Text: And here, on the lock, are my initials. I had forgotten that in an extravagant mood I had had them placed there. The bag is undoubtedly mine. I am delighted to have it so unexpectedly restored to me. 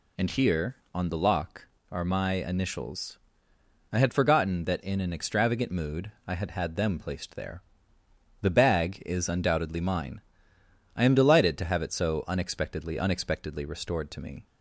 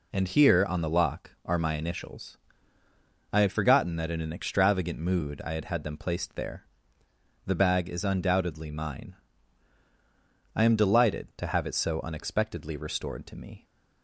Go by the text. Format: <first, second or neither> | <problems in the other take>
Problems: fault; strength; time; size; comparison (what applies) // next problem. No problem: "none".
second | pauses between "mood" and "I"; slight; at 6.1 s; 0.16 s long // says "unexpectedly" twice; at 12.9 s